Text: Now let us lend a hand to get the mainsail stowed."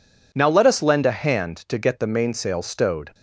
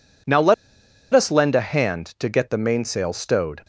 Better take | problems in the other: first | pauses between "let" and "us"; noticeable; at 0.5 s; 0.60 s long

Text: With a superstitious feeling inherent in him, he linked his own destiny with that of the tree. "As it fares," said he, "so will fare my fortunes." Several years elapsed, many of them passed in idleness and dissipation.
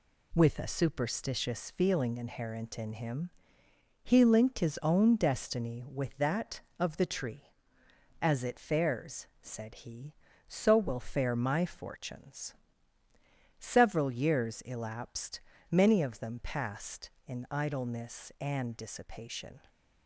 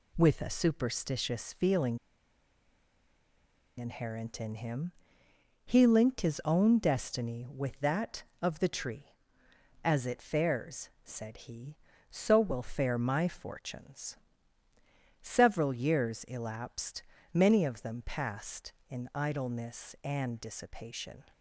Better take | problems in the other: first | pauses between "feeling" and "inherent"; strong; at 1.9 s; 1.7 s long

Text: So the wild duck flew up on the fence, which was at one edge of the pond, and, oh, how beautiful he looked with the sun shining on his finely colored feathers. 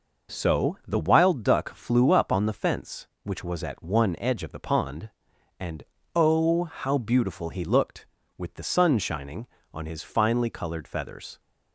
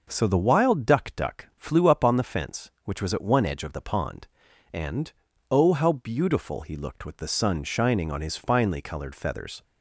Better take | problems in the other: first | starts louder than the rest; noticeable; until 1.1 s; 6 dB // says "duck" twice; at 1.1 s

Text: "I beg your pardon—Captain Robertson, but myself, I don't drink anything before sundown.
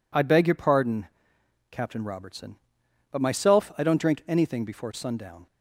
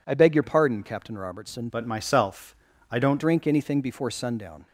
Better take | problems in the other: first | changes voice from "but" to "don't"; from 1.6 to 3.1 s; 1.5 s long

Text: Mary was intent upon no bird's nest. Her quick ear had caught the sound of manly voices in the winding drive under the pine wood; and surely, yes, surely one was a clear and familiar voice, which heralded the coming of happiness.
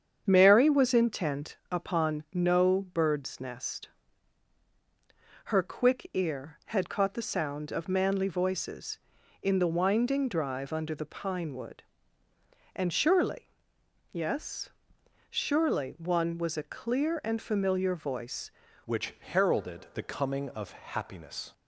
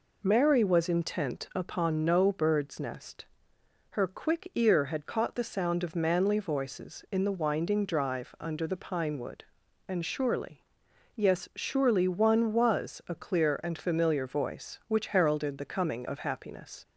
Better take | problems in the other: second | starts louder than the rest; strong; until 1.2 s; 7.5 dB // pauses between "intent" and "upon"; slight; at 1.5 s; 0.16 s long // changes voice at "which"; from 18.8 s on; 2.7 s long

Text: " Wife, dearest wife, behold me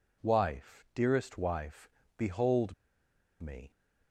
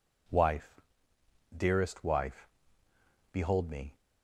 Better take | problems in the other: second | pauses between "behold" and "me"; noticeable; at 2.7 s; 0.68 s long

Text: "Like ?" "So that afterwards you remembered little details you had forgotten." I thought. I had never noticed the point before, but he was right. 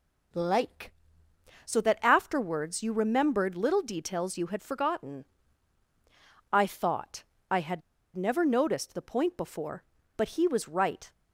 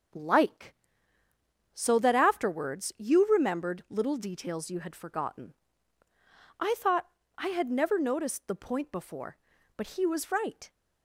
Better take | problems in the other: second | pauses between "had" and "never"; slight; at 7.8 s; 0.34 s long

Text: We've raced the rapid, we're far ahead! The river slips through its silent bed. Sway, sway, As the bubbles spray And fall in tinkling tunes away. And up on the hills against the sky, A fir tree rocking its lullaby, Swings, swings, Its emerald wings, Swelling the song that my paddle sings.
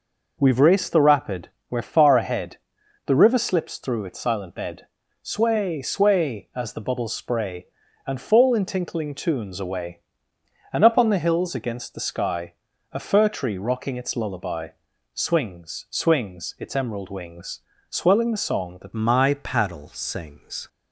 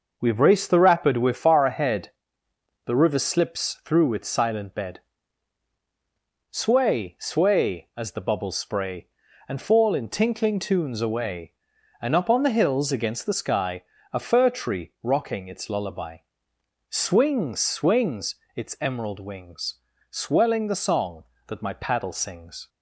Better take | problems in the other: second | changes voice at "my"; from 18.9 s on; 1.7 s long

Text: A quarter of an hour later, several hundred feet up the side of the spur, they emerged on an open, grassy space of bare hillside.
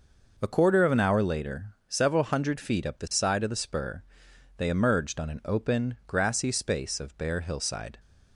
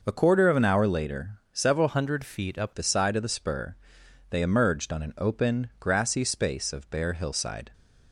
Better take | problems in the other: first | changes voice from "hundred" to "up"; from 1.8 to 2.7 s; 0.9 s long

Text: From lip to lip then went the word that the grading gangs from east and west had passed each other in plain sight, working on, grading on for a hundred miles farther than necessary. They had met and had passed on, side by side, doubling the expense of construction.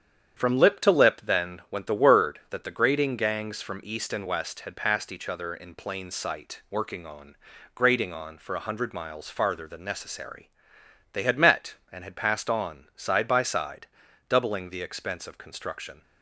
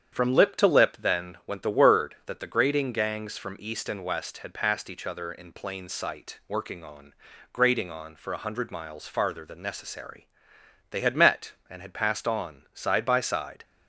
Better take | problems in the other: first | starts louder than the rest; strong; until 1.2 s; 8.5 dB; strong in the first // stops before "doubling the expense of construction"; at 13.6 s

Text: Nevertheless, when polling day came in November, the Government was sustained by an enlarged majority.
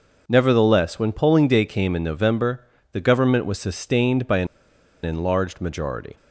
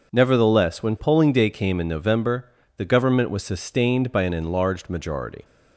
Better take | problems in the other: second | pauses between "an" and "enlarged"; noticeable; at 4.4 s; 0.56 s long

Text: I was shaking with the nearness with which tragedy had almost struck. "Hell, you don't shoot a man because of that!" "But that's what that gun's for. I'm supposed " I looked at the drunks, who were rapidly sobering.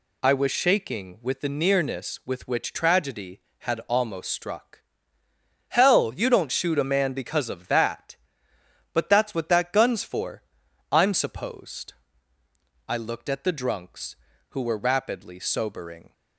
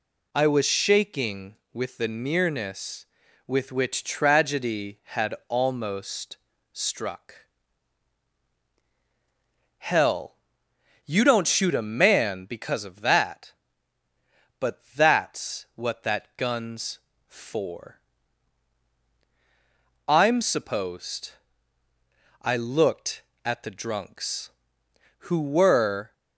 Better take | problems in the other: first | pauses between "almost" and "struck"; slight; at 6.3 s; 0.34 s long // stops before "rapidly sobering"; at 26.1 s

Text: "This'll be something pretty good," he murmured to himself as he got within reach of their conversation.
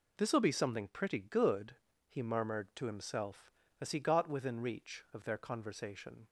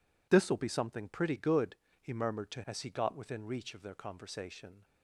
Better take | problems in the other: first | skips "himself"; at 2.6 s

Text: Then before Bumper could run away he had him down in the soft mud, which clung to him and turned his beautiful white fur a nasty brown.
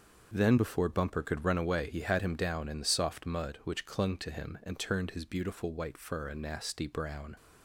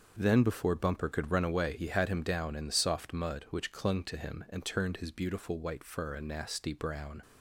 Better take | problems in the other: neither | starts louder than the rest; the same in both

